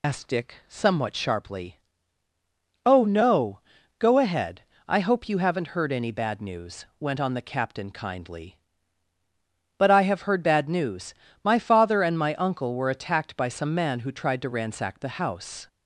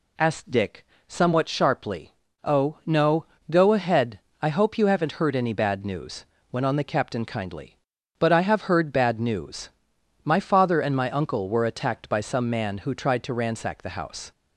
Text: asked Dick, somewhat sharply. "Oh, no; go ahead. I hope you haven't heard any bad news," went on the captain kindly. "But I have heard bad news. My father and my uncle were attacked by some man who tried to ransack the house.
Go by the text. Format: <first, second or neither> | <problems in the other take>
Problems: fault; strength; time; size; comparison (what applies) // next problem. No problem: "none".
second | loses the start of "asked"; at 0.0 s; 60 ms